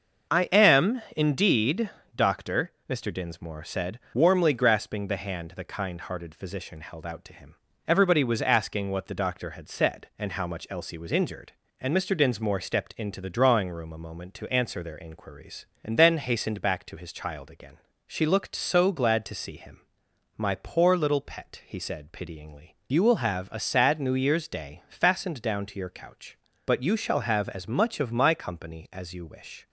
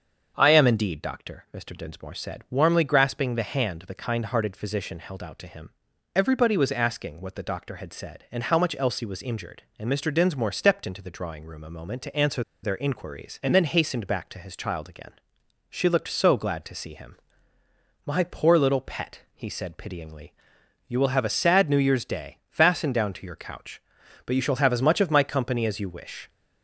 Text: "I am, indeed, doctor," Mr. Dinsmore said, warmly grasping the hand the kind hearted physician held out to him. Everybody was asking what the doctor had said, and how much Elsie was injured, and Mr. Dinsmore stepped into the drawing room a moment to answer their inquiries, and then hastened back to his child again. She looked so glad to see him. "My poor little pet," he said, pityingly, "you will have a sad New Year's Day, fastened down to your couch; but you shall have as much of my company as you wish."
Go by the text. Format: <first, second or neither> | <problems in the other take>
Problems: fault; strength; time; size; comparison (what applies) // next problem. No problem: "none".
first | starts louder than the rest; until 1.3 s; 7 dB; also in the first // pauses between "answer" and "their"; slight; at 12.4 s; 0.21 s long